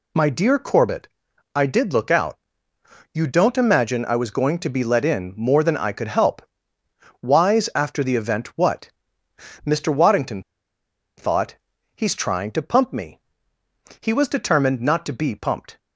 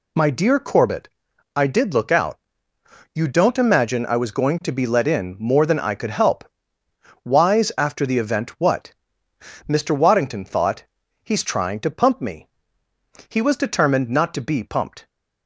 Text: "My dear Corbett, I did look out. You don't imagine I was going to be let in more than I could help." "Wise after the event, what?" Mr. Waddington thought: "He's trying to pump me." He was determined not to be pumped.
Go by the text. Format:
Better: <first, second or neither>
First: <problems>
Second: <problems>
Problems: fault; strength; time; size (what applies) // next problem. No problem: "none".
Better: second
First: pauses between "Waddington" and "thought"; noticeable; at 10.4 s; 0.75 s long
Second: none